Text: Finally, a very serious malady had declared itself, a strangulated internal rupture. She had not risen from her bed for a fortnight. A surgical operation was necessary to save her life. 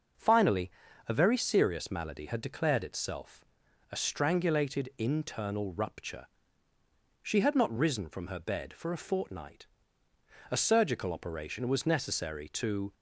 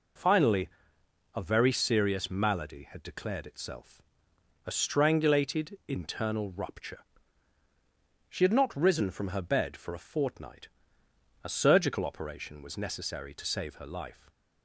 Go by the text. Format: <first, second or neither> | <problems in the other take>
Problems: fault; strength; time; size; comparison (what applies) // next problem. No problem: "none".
second | stops before "save her life"; at 12.9 s